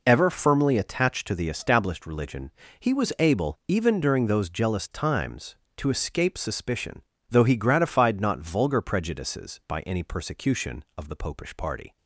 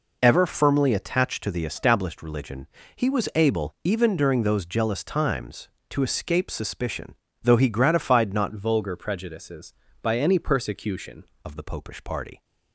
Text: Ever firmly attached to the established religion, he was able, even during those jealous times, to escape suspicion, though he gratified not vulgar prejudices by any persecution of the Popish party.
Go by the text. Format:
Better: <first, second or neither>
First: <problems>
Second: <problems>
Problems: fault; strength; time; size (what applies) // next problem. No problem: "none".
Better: first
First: none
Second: changes voice from "vulgar" to "persecution"; from 8.5 to 11.2 s; 2.7 s long